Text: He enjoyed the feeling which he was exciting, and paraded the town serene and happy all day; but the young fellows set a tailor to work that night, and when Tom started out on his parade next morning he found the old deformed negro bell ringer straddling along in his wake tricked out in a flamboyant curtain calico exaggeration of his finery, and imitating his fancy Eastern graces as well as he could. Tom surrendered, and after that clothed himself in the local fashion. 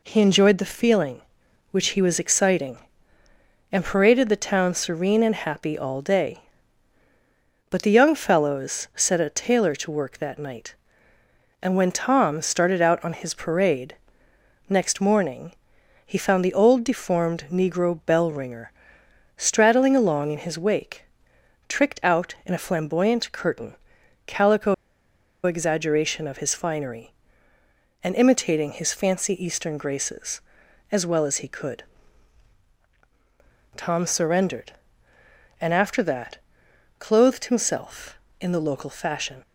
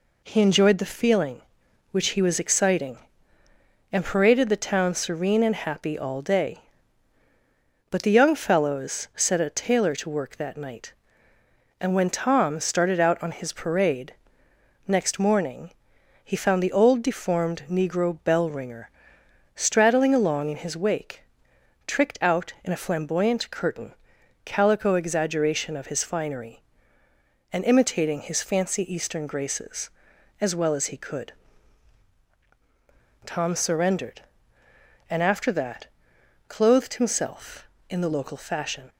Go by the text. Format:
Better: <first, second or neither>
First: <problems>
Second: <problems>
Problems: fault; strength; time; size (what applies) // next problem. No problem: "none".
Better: second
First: pauses between "parade" and "next"; noticeable; at 13.9 s; 0.74 s long // pauses between "morning" and "he"; noticeable; at 15.5 s; 0.52 s long // pauses between "ringer" and "straddling"; noticeable; at 18.7 s; 0.66 s long // pauses between "wake" and "tricked"; noticeable; at 21.0 s; 0.64 s long // pauses between "curtain" and "calico"; noticeable; at 23.7 s; 0.50 s long // pauses between "calico" and "exaggeration"; noticeable; at 24.7 s; 0.70 s long // pauses between "that" and "clothed"; noticeable; at 36.3 s; 0.62 s long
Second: pauses between "parade" and "next"; noticeable; at 14.1 s; 0.74 s long // pauses between "morning" and "he"; noticeable; at 15.7 s; 0.52 s long // pauses between "ringer" and "straddling"; noticeable; at 18.8 s; 0.66 s long // pauses between "wake" and "tricked"; noticeable; at 21.2 s; 0.64 s long // pauses between "curtain" and "calico"; noticeable; at 23.9 s; 0.50 s long // pauses between "that" and "clothed"; noticeable; at 35.8 s; 0.62 s long